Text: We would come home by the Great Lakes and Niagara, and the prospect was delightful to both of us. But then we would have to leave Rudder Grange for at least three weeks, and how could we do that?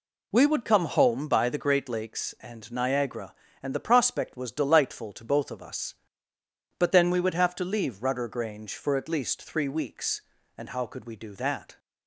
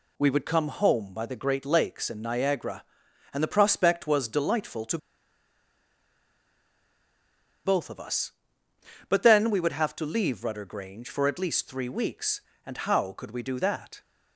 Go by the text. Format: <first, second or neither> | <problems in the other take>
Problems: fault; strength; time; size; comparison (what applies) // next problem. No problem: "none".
first | pauses between "to" and "both"; strong; at 4.9 s; 2.6 s long